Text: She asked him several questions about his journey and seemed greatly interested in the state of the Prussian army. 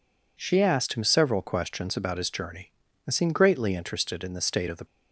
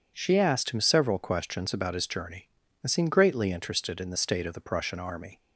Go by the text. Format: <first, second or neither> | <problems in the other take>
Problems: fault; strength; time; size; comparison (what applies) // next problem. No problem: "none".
second | stops before "Prussian army"; at 4.8 s